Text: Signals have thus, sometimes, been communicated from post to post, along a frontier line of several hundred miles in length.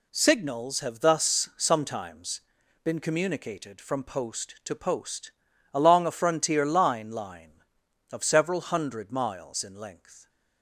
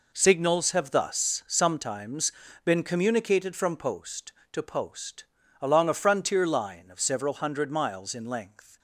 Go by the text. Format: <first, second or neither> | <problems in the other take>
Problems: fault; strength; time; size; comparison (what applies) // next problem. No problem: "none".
second | says "line" twice; at 7.1 s